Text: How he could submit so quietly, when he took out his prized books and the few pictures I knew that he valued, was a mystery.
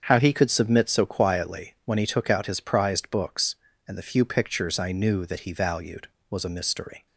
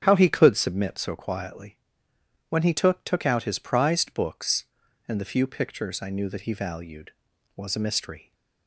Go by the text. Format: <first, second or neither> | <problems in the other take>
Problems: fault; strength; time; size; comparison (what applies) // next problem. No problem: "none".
first | starts louder than the rest; strong; until 1.0 s; 8 dB; strong in the first // says "took" twice; at 3.0 s